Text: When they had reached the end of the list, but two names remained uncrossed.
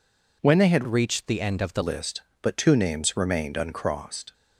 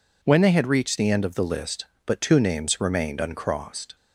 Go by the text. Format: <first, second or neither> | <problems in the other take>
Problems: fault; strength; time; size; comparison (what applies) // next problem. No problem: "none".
second | changes voice from "reached" to "the"; from 0.8 to 1.8 s; 1.0 s long